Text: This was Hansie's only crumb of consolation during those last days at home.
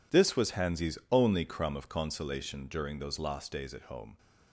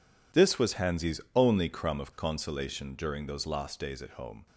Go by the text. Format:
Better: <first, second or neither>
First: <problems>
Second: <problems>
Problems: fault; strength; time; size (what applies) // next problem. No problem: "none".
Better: neither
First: none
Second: none